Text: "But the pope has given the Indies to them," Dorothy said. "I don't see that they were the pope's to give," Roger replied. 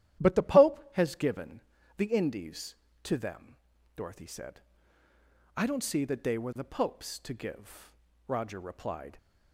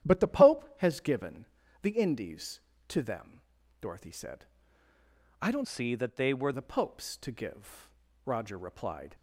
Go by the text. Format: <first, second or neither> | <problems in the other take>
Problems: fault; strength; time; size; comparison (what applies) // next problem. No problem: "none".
first | starts louder than the rest; strong; until 1.1 s; 11 dB; strong in the first // pauses between "given" and "the"; slight; at 1.4 s; 0.36 s long; slight in the first // changes voice from "see" to "were"; from 5.6 to 6.5 s; 0.9 s long